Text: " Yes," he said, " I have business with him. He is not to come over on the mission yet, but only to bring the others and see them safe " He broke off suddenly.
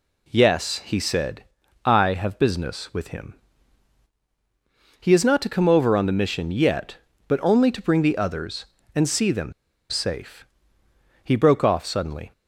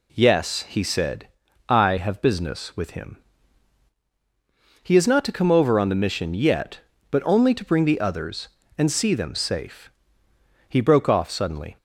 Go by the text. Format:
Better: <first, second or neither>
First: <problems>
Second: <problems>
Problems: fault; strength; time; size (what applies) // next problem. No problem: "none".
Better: second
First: pauses between "them" and "safe"; at 9.5 s; 0.37 s long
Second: none